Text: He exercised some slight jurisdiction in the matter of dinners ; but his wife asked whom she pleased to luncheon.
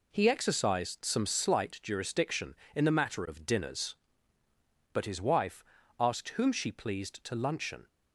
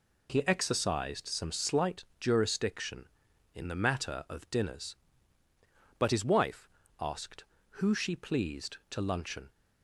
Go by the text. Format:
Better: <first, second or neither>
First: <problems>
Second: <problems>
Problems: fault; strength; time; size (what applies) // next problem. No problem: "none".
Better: first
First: pauses between "wife" and "asked"; slight; at 5.6 s; 0.34 s long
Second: pauses between "slight" and "jurisdiction"; slight; at 2.0 s; 0.16 s long // pauses between "wife" and "asked"; slight; at 6.6 s; 0.32 s long // says "who" for "whom"; at 7.8 s